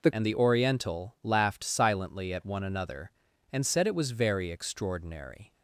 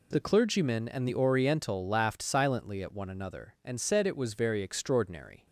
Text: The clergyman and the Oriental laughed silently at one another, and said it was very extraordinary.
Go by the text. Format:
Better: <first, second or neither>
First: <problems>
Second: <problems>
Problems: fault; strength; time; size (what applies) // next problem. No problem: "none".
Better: second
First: skips "clergyman"; at 0.1 s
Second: none